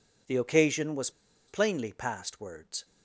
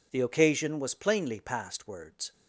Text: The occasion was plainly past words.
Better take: second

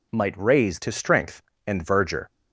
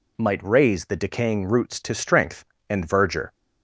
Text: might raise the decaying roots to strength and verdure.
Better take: second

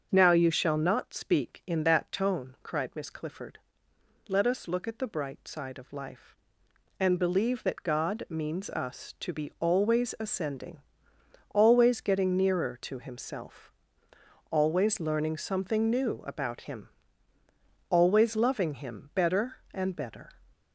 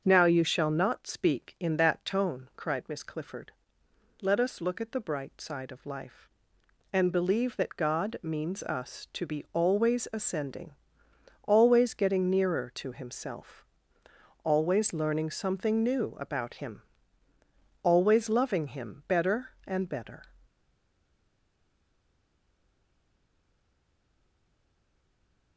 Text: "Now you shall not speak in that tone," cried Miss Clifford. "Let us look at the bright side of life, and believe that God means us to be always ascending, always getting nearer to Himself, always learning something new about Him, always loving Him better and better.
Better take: first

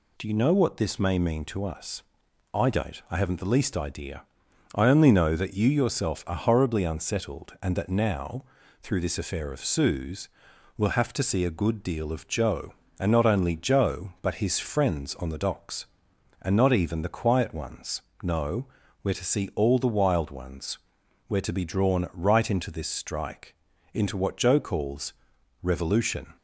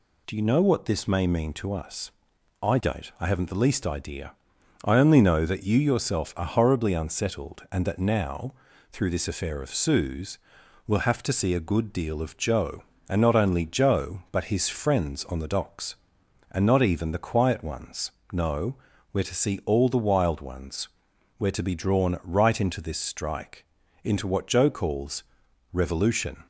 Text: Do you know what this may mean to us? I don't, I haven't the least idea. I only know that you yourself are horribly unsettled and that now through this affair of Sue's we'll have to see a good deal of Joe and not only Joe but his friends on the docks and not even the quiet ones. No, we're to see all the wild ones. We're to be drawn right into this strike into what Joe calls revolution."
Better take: neither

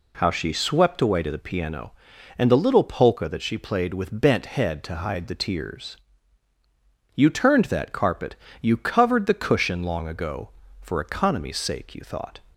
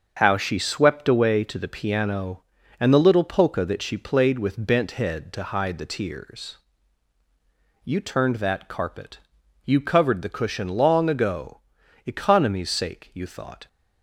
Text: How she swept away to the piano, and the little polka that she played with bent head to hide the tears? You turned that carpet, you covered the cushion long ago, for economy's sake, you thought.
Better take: first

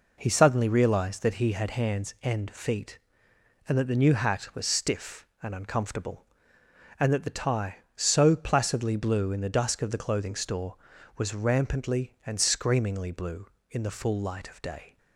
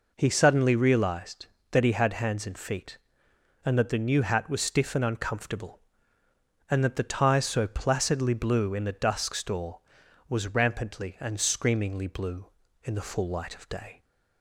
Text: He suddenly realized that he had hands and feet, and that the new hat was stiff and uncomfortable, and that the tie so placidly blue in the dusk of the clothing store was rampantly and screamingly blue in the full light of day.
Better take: first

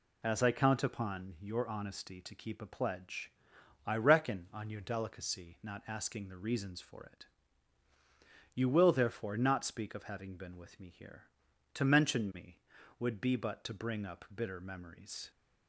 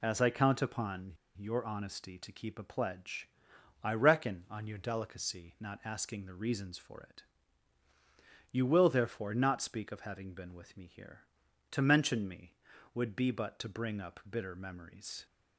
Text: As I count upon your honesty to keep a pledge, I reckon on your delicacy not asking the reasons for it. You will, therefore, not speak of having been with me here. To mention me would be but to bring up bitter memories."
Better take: first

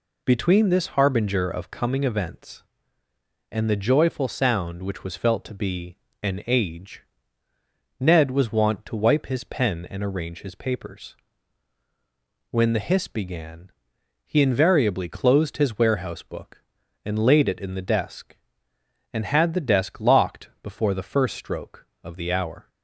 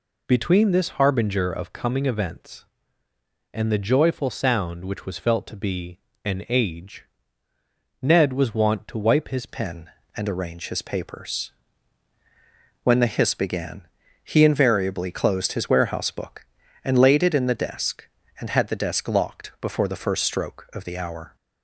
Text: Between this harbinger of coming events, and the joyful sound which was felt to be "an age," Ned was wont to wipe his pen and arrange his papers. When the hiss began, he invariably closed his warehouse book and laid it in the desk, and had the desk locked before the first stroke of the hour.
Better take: first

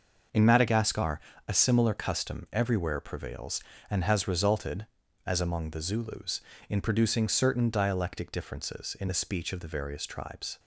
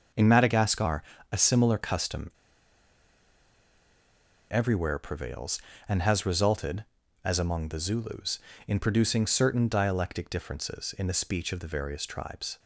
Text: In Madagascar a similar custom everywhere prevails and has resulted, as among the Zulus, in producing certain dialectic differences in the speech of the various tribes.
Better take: first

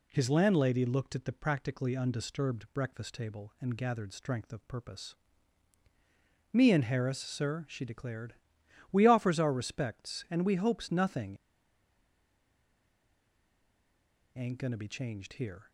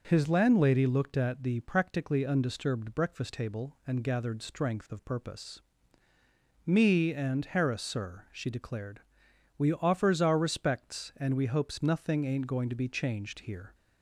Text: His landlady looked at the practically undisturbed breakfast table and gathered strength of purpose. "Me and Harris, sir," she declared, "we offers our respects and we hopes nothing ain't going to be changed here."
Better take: second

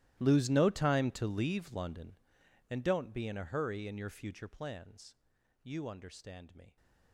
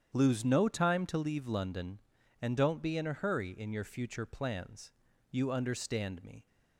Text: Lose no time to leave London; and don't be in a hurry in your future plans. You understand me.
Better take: second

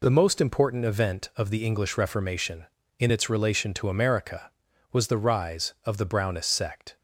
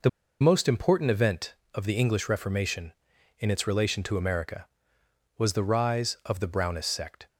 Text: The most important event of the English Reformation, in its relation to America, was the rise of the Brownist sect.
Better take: first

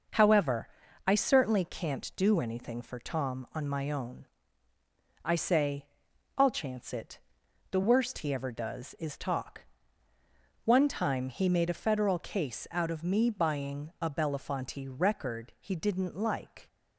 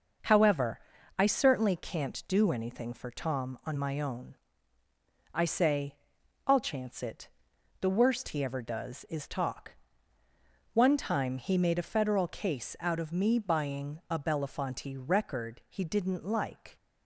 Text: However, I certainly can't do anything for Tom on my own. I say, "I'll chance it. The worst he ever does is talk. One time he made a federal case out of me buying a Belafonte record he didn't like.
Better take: neither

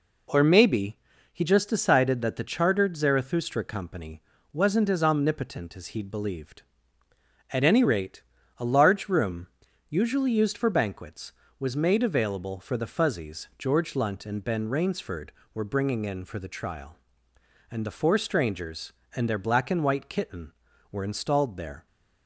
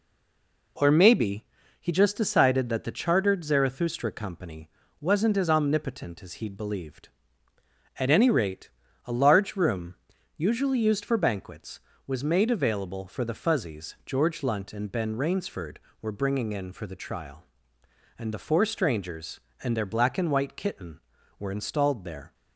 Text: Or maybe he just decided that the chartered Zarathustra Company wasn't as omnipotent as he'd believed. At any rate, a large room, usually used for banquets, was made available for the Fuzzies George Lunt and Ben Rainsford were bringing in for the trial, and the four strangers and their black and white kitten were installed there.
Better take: first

